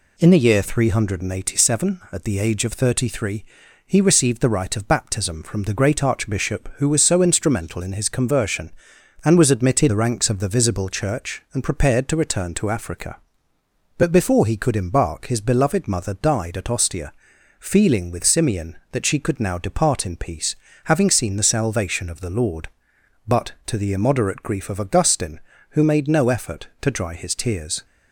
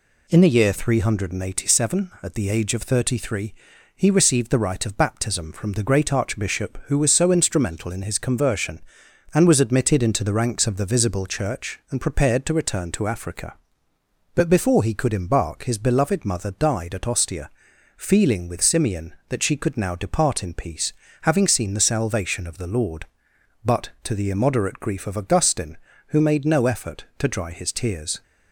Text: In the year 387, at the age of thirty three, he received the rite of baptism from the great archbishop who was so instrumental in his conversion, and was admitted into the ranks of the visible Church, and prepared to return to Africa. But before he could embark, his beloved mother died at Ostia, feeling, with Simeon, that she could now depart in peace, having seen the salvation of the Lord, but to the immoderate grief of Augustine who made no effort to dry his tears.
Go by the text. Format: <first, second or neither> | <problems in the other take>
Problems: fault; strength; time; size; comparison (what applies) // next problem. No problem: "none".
second | skips "into"; at 9.8 s